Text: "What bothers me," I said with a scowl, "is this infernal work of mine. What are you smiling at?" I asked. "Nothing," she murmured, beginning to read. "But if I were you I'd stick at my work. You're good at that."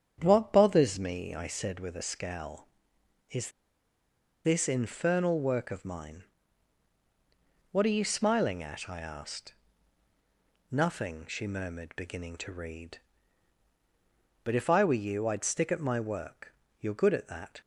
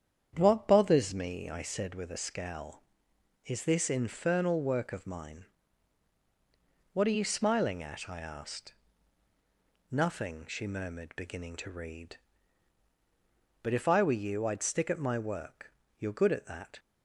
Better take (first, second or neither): second